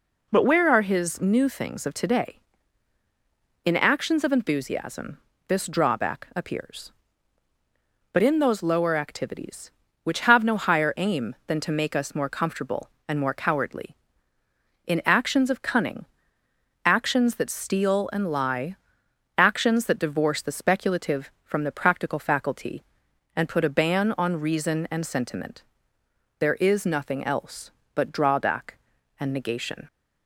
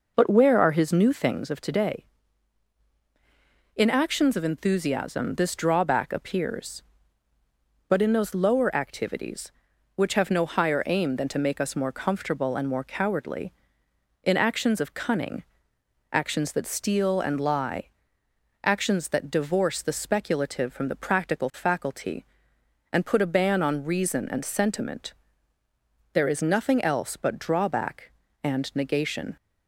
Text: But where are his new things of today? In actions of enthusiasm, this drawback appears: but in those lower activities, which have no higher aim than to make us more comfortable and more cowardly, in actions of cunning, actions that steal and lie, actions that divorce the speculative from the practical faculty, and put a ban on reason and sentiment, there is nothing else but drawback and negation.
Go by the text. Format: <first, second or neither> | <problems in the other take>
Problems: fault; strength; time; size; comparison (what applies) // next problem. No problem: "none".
first | starts louder than the rest; noticeable; until 1.4 s; 5 dB